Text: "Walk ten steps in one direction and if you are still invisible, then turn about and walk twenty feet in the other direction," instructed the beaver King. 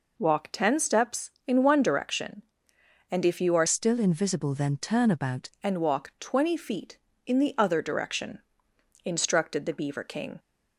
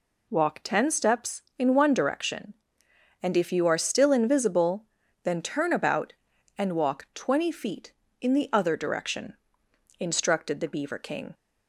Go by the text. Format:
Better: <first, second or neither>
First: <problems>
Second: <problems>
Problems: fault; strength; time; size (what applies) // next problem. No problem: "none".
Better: second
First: changes voice from "still" to "about"; from 3.6 to 5.5 s; 1.9 s long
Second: none